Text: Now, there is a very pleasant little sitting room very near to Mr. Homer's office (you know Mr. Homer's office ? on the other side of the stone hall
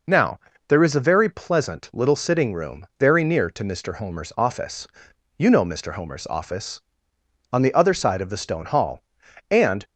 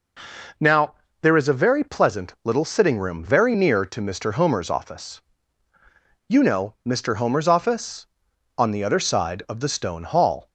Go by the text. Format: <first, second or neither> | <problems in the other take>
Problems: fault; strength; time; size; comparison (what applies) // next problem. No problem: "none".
second | goes on to say "and"; slight; from 9.5 s on; 0.34 s long